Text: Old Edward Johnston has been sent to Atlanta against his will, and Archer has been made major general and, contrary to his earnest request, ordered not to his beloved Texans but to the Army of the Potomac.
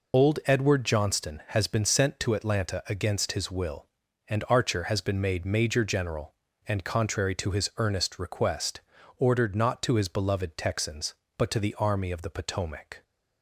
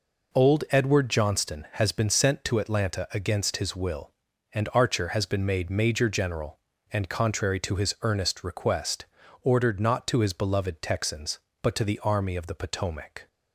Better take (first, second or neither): second